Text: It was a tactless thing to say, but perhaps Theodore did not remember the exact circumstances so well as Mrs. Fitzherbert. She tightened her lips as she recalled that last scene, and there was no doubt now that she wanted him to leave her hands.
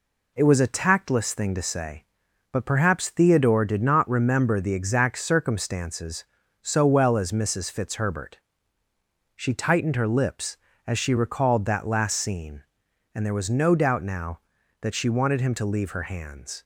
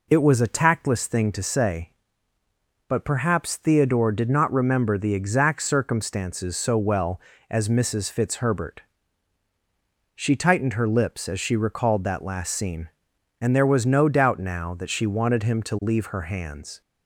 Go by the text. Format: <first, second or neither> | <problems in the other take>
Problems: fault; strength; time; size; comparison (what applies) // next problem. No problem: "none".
neither | none